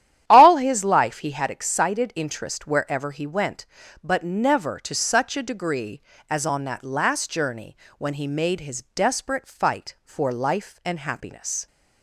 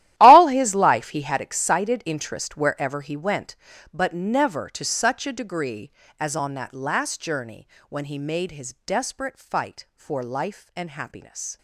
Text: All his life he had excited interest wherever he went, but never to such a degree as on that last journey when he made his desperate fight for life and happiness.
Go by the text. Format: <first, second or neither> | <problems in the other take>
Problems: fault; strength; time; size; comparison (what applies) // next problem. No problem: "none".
first | gets quieter; strong; throughout; 16.5 dB // starts louder than the rest; strong; until 1.1 s; 14 dB; strong in the first // pauses between "journey" and "when"; slight; at 7.6 s; 0.22 s long; slight in the first